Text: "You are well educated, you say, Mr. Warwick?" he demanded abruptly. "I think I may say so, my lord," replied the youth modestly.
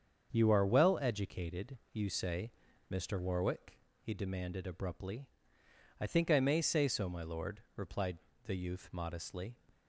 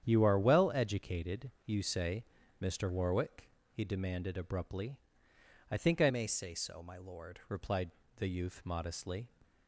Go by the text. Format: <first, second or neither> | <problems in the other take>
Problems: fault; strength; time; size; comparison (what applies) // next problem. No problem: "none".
first | starts louder than the rest; strong; until 1.1 s; 8.5 dB; also in the first // changes voice from "may" to "lord"; from 6.0 to 7.3 s; 1.3 s long // pauses between "replied" and "the"; slight; at 7.8 s; 0.28 s long; slight in the first